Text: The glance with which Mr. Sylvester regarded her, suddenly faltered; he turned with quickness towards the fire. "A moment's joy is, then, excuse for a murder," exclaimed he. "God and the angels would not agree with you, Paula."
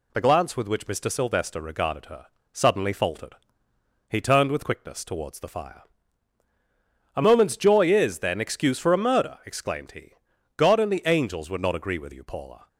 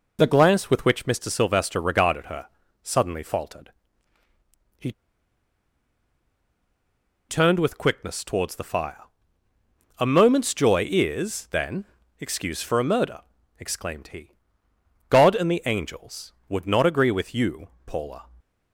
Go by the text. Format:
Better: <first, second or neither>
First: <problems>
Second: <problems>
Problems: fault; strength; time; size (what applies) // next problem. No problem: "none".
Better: first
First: none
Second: pauses between "he" and "turned"; strong; at 4.9 s; 2.3 s long